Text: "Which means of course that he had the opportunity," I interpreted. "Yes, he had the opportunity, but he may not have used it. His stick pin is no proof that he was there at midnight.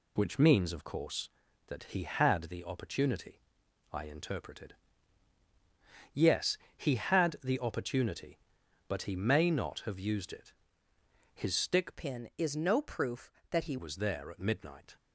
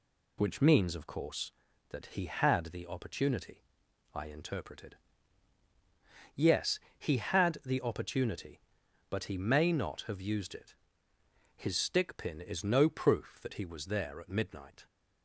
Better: second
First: changes voice from "pin" to "he"; from 11.9 to 13.7 s; 1.8 s long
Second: none

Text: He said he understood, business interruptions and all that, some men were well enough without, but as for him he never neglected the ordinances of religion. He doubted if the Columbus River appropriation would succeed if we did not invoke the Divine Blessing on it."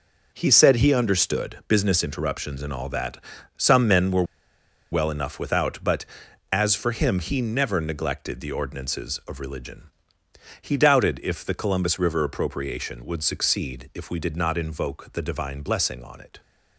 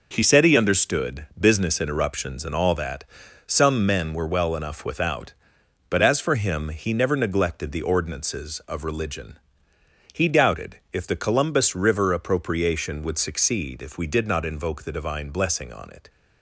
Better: second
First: pauses between "were" and "well"; noticeable; at 4.2 s; 0.68 s long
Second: none

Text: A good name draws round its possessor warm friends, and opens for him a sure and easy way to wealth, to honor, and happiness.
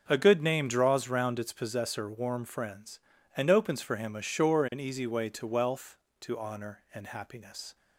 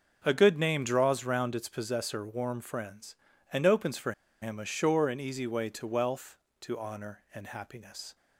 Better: first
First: starts louder than the rest; until 1.1 s; 6 dB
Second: starts louder than the rest; until 1.2 s; 6 dB // pauses between "for" and "him"; slight; at 4.1 s; 0.30 s long

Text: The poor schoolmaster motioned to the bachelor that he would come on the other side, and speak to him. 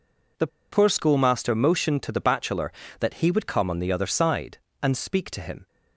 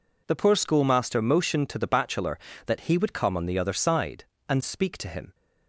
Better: second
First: pauses between "The" and "poor"; slight; at 0.4 s; 0.24 s long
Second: none

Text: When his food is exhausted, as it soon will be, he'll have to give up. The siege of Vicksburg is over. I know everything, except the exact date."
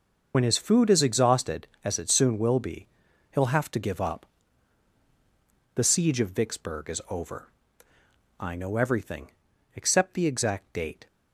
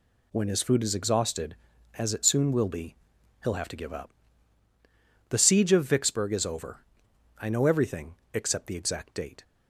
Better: second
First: loses the start of "When"; at 0.3 s; 60 ms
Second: none

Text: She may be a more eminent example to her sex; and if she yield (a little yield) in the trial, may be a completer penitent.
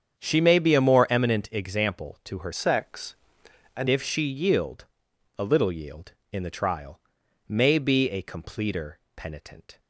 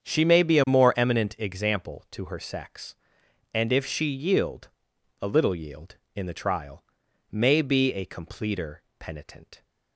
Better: second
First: starts louder than the rest; strong; until 1.2 s; 8 dB // changes voice from "sex" to "and"; from 2.5 to 3.8 s; 1.3 s long // pauses between "completer" and "penitent"; slight; at 8.9 s; 0.16 s long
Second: starts louder than the rest; strong; until 1.0 s; 8 dB // pauses between "completer" and "penitent"; slight; at 8.8 s; 0.16 s long

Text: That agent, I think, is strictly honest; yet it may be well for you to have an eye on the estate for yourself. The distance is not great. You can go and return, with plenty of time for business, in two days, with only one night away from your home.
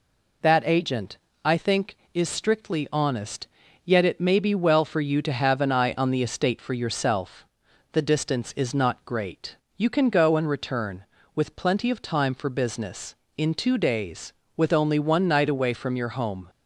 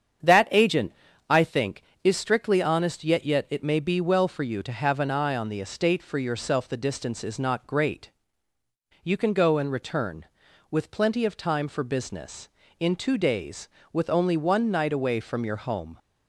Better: first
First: none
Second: starts louder than the rest; strong; until 1.6 s; 8 dB // says "yet" twice; at 3.2 s

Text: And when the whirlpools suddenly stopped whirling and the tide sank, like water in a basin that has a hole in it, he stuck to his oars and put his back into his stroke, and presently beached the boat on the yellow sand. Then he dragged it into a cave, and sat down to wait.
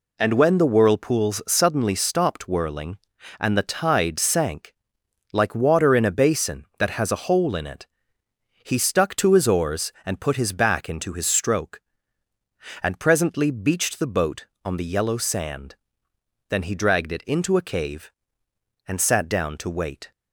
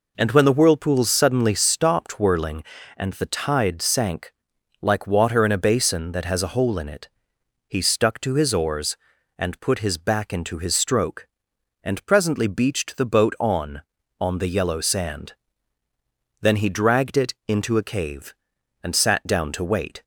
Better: first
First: none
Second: says "on" twice; at 14.2 s

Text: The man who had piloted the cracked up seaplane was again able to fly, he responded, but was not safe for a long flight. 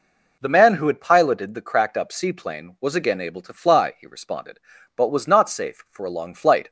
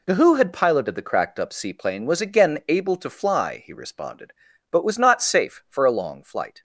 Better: first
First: none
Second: skips "man"; at 0.1 s

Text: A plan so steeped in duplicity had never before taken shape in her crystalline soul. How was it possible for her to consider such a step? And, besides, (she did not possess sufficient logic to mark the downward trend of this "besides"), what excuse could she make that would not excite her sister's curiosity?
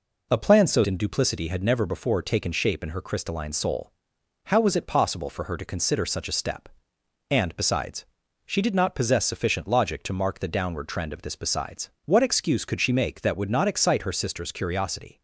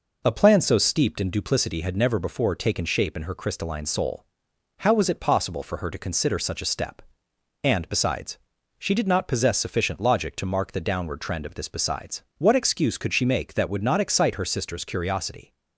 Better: second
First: skips "steeped"; at 0.8 s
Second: none

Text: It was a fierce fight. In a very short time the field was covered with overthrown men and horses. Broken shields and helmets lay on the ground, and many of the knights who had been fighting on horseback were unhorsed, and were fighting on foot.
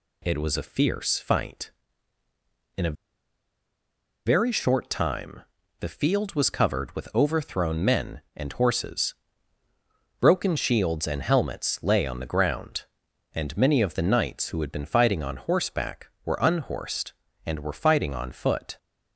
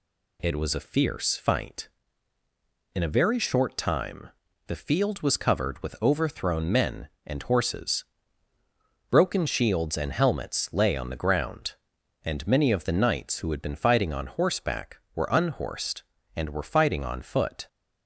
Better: second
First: pauses between "a" and "very"; strong; at 2.9 s; 1.3 s long // pauses between "time" and "the"; at 5.4 s; 0.38 s long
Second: pauses between "time" and "the"; at 4.2 s; 0.38 s long

